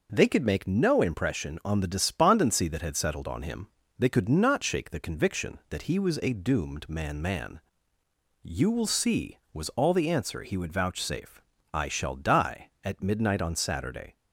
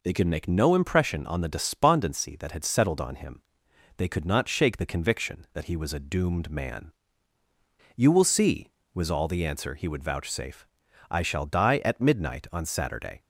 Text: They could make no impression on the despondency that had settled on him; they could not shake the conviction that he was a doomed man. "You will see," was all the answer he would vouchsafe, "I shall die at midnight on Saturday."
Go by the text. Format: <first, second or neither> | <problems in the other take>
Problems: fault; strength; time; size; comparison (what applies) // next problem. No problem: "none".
second | says "man" twice; at 7.2 s